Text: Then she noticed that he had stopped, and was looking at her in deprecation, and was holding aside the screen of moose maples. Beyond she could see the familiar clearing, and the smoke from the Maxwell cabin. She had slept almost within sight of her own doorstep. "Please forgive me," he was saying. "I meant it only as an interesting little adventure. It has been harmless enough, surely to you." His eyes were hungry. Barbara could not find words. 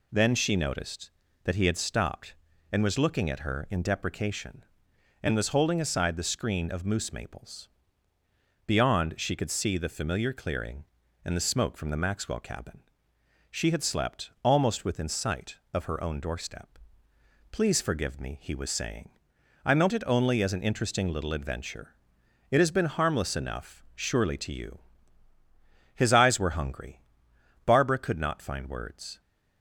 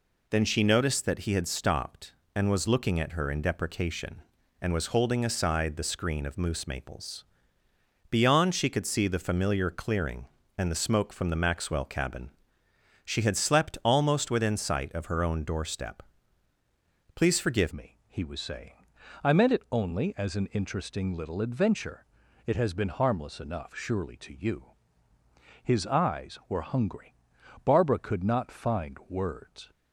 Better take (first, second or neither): first